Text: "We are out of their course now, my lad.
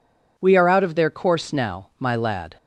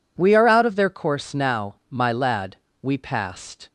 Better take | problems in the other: first | goes on to say "We passed"; noticeable; from 2.8 s on; 0.88 s long

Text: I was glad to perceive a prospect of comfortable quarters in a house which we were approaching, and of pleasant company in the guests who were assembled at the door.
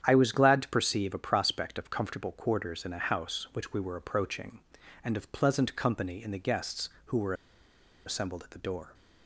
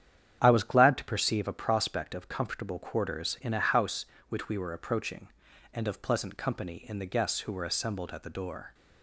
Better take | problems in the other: second | starts louder than the rest; strong; until 1.0 s; 9 dB; strong in the second // pauses between "were" and "assembled"; noticeable; at 7.3 s; 0.72 s long

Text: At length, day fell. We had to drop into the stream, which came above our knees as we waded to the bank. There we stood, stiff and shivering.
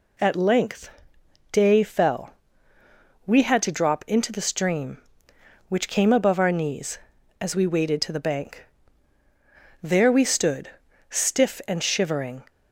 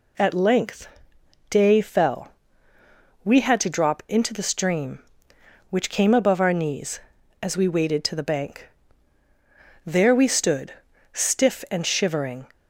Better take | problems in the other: neither | none

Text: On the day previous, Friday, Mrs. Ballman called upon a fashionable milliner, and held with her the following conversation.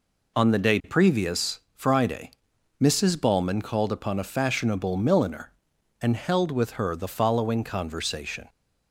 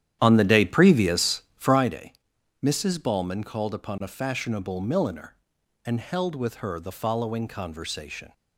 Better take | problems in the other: first | starts louder than the rest; strong; until 1.9 s; 10.5 dB

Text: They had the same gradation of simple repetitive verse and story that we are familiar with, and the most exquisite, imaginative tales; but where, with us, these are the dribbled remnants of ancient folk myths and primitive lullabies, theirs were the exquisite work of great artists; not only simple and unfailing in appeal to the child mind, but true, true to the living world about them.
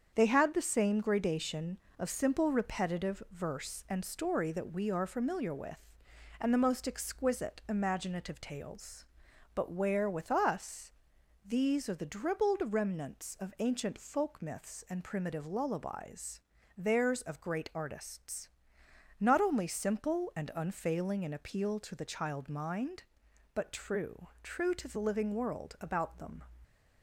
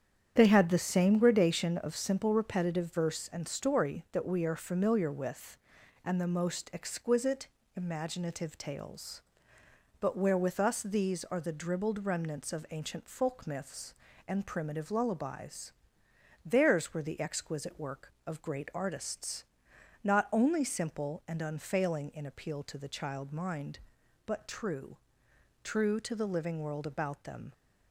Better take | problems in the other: second | starts louder than the rest; strong; until 1.1 s; 7.5 dB; strong in the second // skips "were the exquisite work"; at 17.2 s

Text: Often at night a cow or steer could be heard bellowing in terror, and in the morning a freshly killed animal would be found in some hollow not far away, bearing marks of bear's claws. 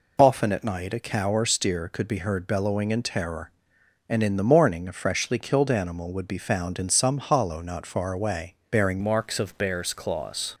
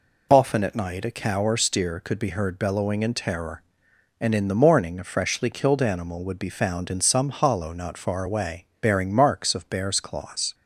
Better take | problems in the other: second | changes voice at "marks"; from 9.0 s on; 1.5 s long

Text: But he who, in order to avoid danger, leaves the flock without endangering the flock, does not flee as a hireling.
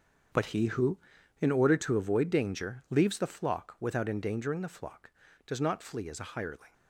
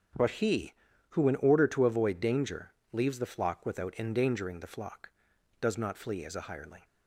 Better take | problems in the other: second | gets quieter; strong; throughout; 13 dB // starts louder than the rest; strong; until 1.7 s; 7 dB; also in the second

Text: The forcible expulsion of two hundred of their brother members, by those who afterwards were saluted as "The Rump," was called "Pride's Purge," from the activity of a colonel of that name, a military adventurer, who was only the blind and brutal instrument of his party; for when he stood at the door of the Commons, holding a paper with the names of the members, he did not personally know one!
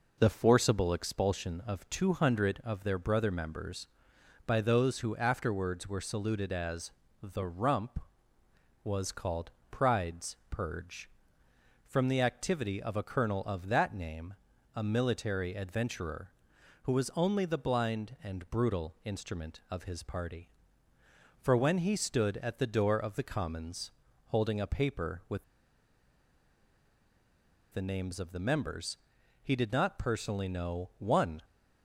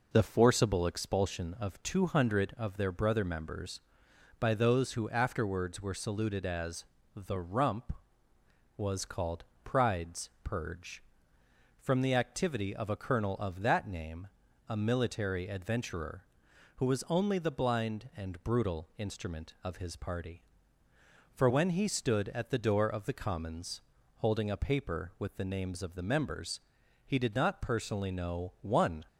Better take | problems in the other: second | pauses between "as" and "The"; slight; at 6.9 s; 0.32 s long; slight in the second // pauses between "called" and "Pride's"; slight; at 9.5 s; 0.20 s long; slight in the second // pauses between "Pride's" and "Purge"; slight; at 10.3 s; 0.16 s long; slight in the second // pauses between "with" and "the"; strong; at 25.4 s; 2.2 s long

